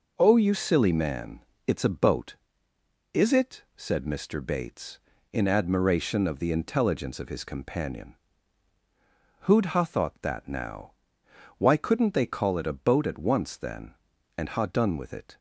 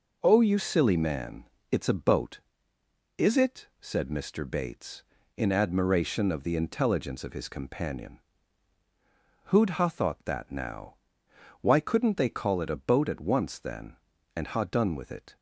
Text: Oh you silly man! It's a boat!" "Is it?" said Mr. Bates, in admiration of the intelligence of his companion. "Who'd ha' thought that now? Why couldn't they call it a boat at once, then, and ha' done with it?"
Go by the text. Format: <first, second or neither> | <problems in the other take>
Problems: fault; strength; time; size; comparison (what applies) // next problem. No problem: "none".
neither | none